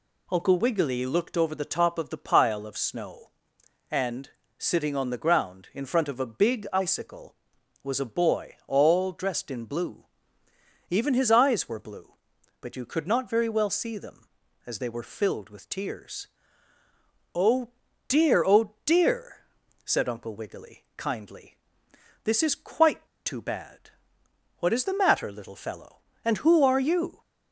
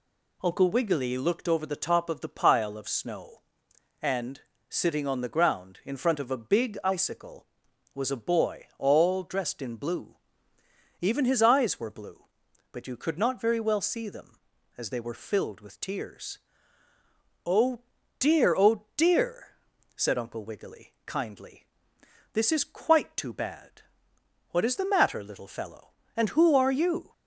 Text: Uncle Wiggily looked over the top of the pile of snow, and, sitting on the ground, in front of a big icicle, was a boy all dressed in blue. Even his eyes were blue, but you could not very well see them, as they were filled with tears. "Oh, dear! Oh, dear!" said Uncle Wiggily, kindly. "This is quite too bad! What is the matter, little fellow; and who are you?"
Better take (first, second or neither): second